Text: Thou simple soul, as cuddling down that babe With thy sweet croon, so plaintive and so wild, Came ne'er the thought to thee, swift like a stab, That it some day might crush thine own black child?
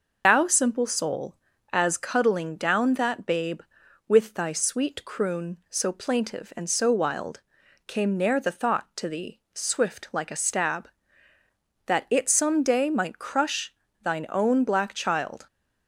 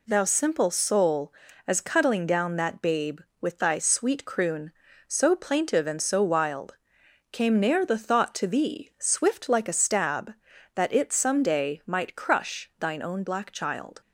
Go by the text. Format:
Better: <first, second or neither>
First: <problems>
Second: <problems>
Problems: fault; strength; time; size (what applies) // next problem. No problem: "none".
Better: second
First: loses the start of "Thou"; at 0.2 s; 110 ms // pauses between "crush" and "thine"; slight; at 13.7 s; 0.30 s long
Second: none